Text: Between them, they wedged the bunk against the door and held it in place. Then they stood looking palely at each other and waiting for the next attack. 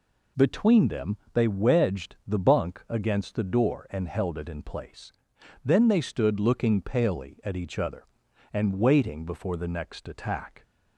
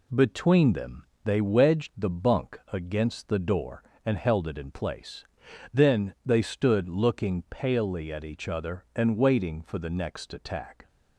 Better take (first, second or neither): second